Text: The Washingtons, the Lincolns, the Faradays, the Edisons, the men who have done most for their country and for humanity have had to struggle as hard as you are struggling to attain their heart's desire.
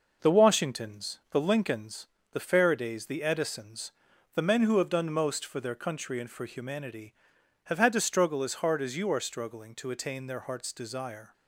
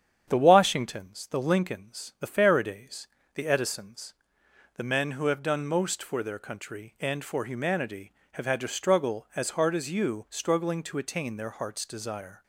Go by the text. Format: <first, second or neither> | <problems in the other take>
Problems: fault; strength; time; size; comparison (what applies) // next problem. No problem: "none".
first | starts louder than the rest; strong; until 1.3 s; 8.5 dB // skips "are"; at 10.2 s